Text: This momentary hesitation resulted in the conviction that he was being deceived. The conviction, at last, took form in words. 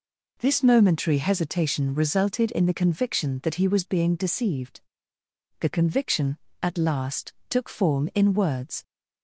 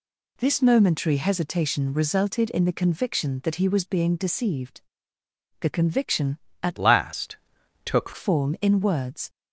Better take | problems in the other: first | changes voice from "last" to "took"; from 6.7 to 8.1 s; 1.4 s long

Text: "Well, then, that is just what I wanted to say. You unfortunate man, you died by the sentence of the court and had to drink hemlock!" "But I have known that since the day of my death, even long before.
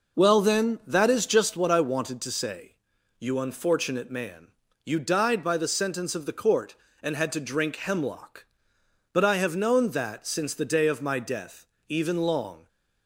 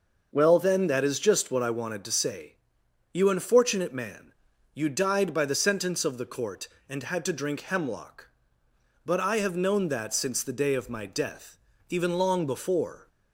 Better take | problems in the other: second | stops before "before"; at 12.6 s

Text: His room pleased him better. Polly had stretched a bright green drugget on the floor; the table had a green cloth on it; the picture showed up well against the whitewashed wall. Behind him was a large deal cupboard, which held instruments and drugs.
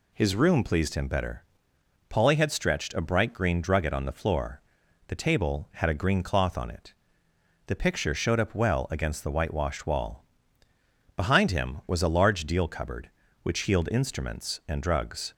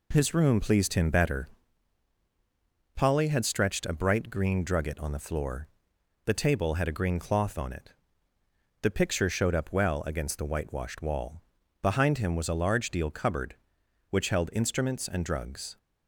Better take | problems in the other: second | says "healed" for "held"; at 13.6 s

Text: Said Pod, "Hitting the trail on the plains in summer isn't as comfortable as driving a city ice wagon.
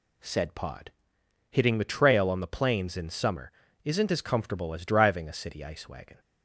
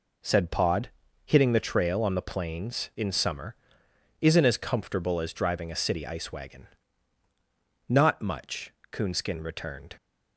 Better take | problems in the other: first | pauses between "summer" and "isn't"; noticeable; at 3.5 s; 0.66 s long; slight in the first // goes on to say "Not much Coonskin returned"; strong; from 7.8 s on; 2.0 s long

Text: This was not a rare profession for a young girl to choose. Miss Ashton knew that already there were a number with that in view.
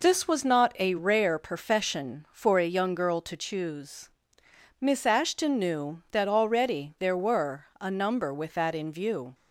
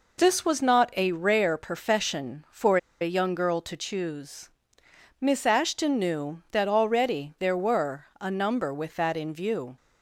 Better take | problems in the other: first | pauses between "for" and "a"; slight; at 2.7 s; 0.23 s long // pauses between "were" and "a"; slight; at 8.0 s; 0.16 s long; slight in the first

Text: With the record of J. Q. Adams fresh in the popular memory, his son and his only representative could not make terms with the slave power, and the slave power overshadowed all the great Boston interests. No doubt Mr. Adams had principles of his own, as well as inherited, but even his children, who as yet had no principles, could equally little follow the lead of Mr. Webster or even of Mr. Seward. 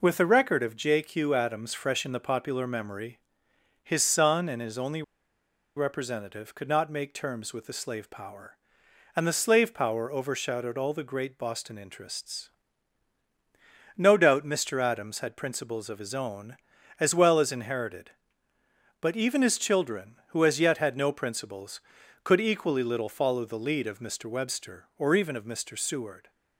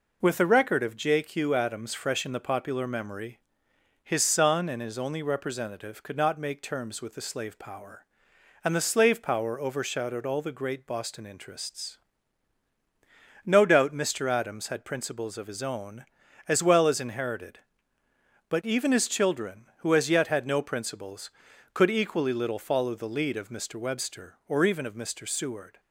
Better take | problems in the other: second | pauses between "only" and "representative"; noticeable; at 5.0 s; 0.74 s long

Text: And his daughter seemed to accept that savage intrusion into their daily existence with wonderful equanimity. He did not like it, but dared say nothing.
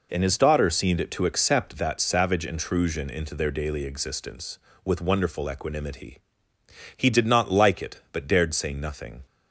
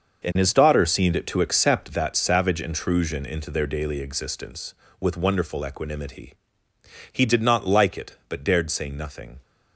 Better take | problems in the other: first | gets quieter; strong; throughout; 10.5 dB

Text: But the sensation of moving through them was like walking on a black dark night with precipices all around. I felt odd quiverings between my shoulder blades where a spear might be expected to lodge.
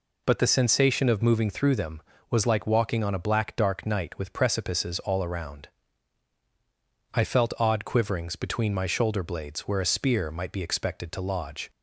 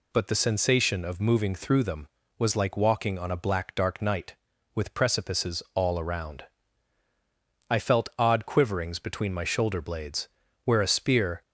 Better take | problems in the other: first | pauses between "blades" and "where"; at 10.2 s; 0.38 s long // stops before "might be expected to lodge"; at 11.4 s

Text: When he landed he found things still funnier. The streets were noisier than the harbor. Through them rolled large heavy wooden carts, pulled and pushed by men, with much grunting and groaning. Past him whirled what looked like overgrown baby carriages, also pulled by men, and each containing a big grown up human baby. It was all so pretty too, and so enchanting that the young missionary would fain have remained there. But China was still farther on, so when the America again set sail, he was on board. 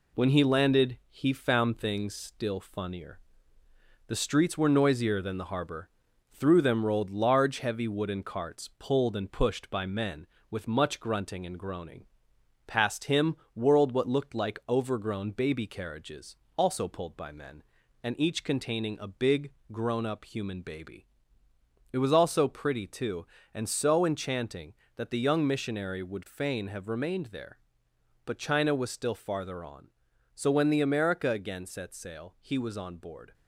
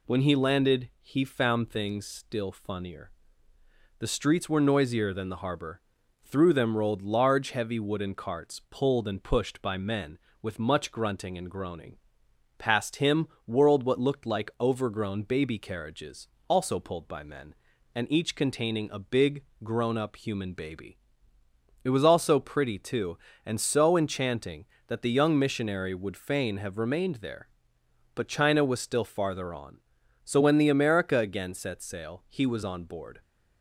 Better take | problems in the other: second | gets quieter; throughout; 3.5 dB // pauses between "him" and "whirled"; slight; at 13.3 s; 0.18 s long; slight in the second // pauses between "big" and "grown"; slight; at 19.5 s; 0.20 s long; slight in the second

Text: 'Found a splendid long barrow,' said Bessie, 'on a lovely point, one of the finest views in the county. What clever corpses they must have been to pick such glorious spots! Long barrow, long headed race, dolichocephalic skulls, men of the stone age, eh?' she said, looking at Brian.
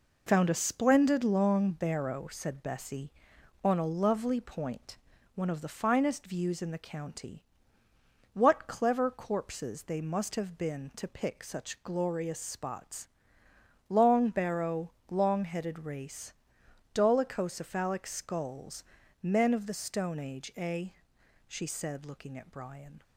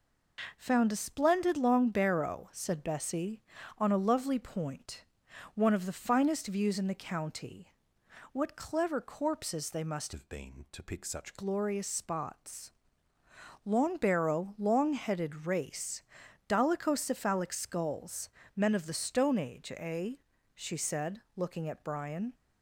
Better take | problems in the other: first | changes voice from "have" to "such"; from 10.1 to 11.3 s; 1.2 s long

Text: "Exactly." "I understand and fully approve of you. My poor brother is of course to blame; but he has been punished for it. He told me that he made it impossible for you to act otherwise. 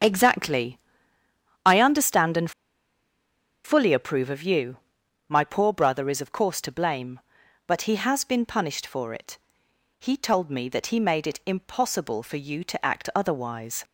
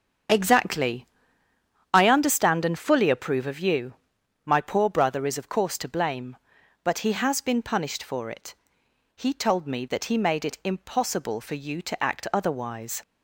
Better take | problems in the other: second | starts louder than the rest; strong; until 1.8 s; 7.5 dB; strong in the second // pauses between "and" and "fully"; at 2.5 s; 1.1 s long

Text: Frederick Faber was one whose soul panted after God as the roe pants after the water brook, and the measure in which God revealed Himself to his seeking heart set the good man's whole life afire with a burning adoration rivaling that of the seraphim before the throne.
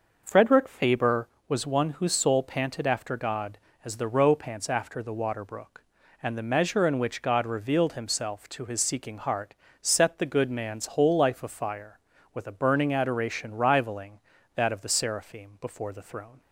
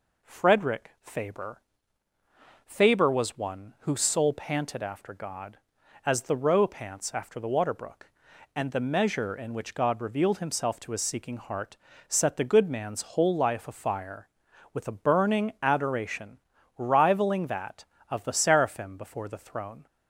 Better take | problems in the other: first | says "Faber" twice; at 2.6 s // pauses between "heart" and "set"; slight; at 11.7 s; 0.32 s long; slight in the first // pauses between "adoration" and "rivaling"; at 16.3 s; 0.40 s long

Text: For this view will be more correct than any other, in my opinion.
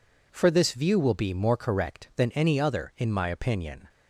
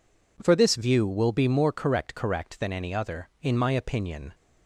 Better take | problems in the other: first | says "correct" twice; at 2.1 s

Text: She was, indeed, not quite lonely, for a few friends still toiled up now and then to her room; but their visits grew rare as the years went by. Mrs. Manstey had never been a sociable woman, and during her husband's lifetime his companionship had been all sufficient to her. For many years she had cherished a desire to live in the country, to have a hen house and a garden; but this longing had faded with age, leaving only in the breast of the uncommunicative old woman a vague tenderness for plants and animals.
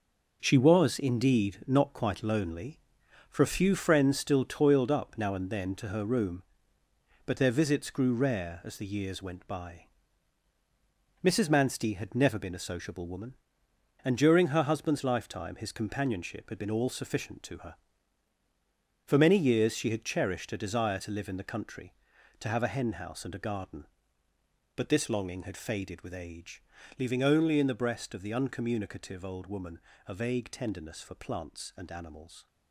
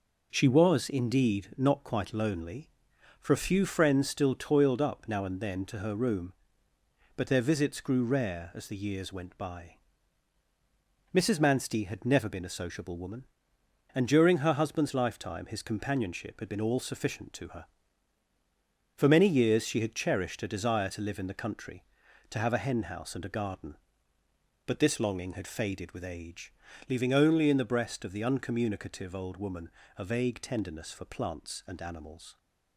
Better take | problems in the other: second | gets quieter; strong; throughout; 8 dB // pauses between "woman" and "a"; slight; at 29.7 s; 0.28 s long; slight in the second

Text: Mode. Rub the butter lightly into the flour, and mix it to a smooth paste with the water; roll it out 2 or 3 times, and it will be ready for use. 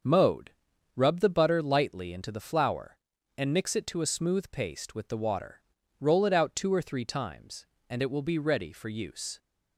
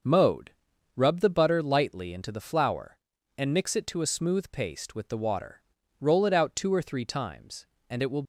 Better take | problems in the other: first | starts louder than the rest; until 1.5 s; 6.5 dB; also in the first // stops before "be ready for use"; at 8.2 s

